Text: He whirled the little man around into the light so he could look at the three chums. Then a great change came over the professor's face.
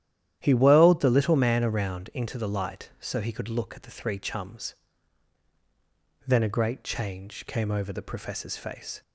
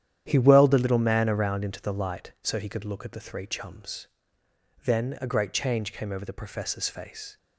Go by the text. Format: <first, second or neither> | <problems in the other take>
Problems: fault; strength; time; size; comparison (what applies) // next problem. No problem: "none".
neither | starts louder than the rest; strong; the same in both